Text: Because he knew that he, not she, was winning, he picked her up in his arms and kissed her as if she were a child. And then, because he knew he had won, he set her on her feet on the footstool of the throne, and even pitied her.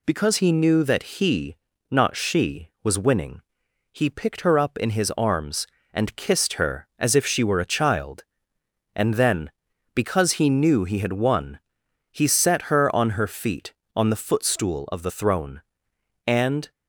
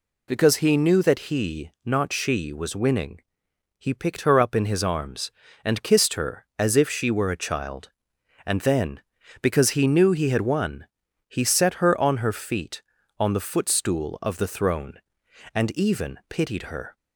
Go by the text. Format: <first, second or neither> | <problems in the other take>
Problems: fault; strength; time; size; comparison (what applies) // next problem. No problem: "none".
second | stops before "even pitied her"; at 16.7 s